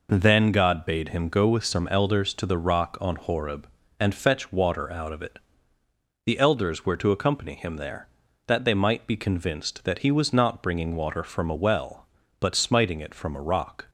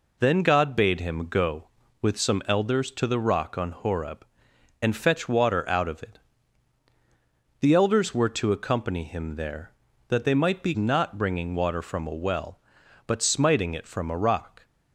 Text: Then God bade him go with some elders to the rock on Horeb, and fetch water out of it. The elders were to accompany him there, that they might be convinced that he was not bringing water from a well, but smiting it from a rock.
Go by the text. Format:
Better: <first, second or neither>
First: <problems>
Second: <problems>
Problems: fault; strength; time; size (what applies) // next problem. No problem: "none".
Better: first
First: none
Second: skips "convinced that he was"; at 10.7 s